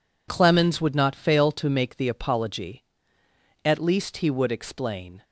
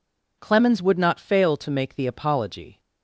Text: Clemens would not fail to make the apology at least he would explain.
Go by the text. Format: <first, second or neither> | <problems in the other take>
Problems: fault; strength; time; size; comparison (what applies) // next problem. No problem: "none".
first | stops before "at least he would explain"; at 2.7 s